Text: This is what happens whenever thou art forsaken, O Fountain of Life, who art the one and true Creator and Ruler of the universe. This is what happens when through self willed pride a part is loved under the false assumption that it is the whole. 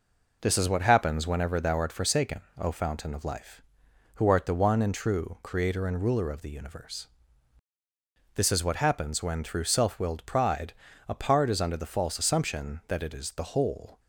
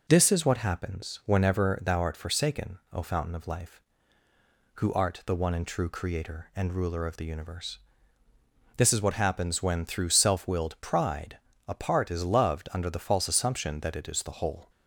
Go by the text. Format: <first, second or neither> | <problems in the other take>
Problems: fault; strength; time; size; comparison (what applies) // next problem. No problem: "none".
second | pauses between "pride" and "a"; at 10.7 s; 0.38 s long; slight in the second // skips "loved"; at 11.5 s